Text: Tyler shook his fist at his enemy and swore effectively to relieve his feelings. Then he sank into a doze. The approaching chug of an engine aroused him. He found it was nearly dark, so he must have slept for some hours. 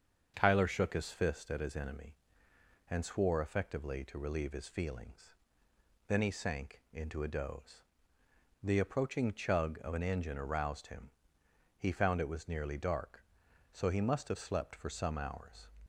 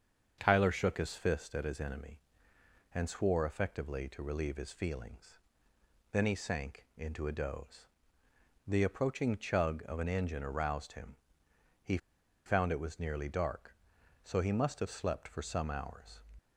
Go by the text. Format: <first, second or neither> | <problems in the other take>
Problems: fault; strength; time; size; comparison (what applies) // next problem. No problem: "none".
first | starts louder than the rest; until 1.4 s; 7 dB; also in the first // pauses between "He" and "found"; noticeable; at 11.9 s; 0.48 s long